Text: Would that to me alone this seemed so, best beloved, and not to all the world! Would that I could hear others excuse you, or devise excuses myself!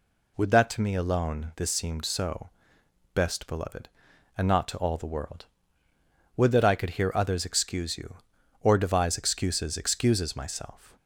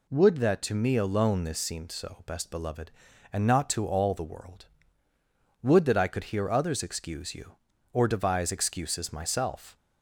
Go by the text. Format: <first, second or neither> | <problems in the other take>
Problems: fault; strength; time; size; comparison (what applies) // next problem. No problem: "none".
second | says "excuses" twice; at 9.7 s